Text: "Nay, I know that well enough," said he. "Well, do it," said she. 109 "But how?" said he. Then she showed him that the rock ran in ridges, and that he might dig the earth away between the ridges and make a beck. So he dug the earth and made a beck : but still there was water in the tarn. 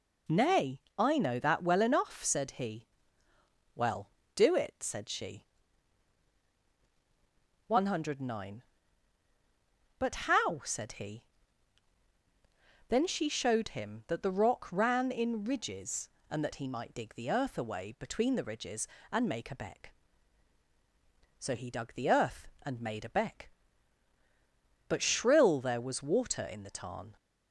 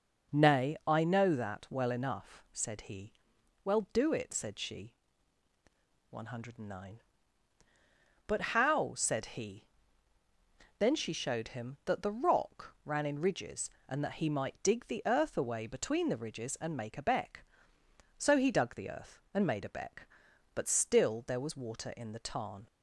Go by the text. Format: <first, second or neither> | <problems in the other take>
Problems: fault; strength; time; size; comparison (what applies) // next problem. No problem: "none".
second | says "shrill" for "still"; at 25.0 s